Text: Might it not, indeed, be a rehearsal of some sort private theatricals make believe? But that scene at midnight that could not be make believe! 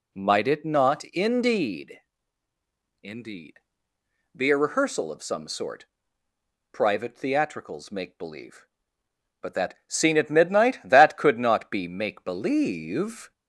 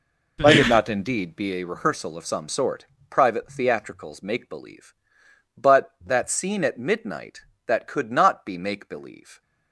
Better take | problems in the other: second | says "indeed" twice; at 3.0 s // pauses between "sort" and "private"; noticeable; at 5.8 s; 0.88 s long; slight in the second

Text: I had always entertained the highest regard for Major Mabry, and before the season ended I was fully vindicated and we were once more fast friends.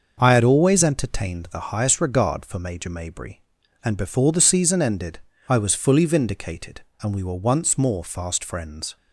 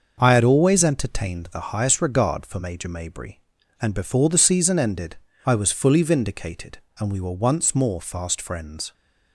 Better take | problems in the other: neither | starts louder than the rest; the same in both // pauses between "ended" and "I"; slight; the same in both

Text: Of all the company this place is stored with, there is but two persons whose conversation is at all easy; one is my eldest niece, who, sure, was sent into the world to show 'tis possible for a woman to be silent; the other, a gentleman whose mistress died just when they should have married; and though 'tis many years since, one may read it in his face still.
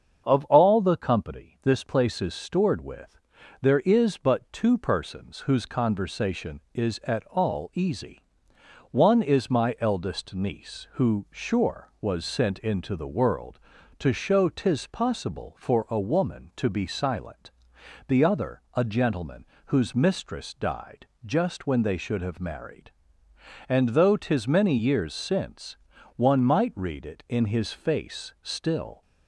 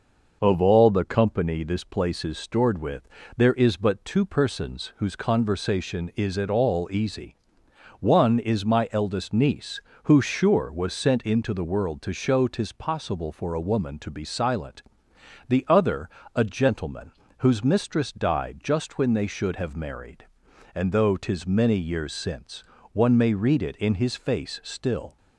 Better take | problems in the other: second | starts louder than the rest; until 1.2 s; 7 dB // pauses between "gentleman" and "whose"; slight; at 19.4 s; 0.20 s long; slight in the second // pauses between "died" and "just"; slight; at 21.0 s; 0.20 s long // says "might" for "may"; at 26.4 s

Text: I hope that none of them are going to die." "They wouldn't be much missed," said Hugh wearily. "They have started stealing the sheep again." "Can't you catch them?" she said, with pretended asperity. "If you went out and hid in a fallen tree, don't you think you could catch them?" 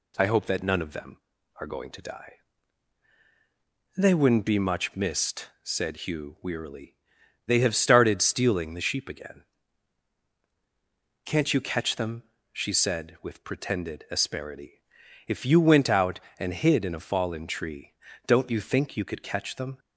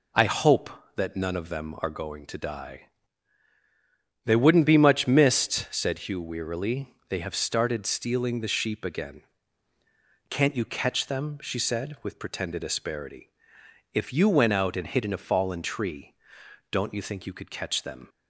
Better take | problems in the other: neither | none

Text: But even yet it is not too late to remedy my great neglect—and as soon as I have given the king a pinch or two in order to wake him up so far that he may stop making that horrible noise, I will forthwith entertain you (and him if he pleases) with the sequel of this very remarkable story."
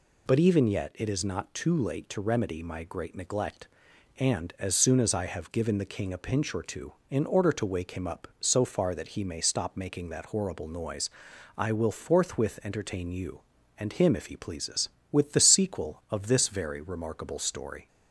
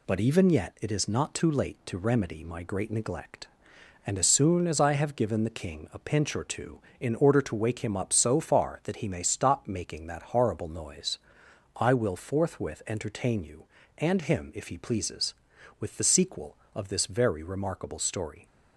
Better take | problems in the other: neither | none

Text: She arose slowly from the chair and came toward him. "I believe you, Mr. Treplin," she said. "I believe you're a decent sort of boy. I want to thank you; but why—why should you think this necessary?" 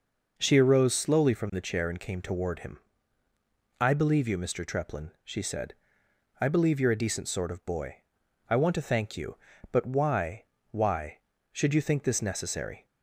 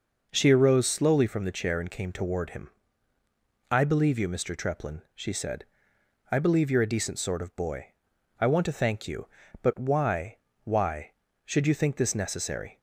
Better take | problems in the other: neither | none

